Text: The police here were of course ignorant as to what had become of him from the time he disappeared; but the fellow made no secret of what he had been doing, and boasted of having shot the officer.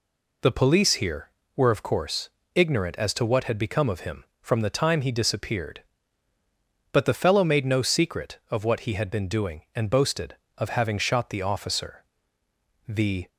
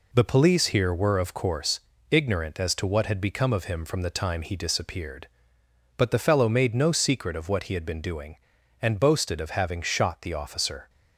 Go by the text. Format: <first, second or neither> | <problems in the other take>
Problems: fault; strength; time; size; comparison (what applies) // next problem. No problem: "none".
second | pauses between "course" and "ignorant"; slight; at 2.2 s; 0.24 s long; slight in the second // goes on to say "The"; slight; from 12.8 s on; 0.40 s long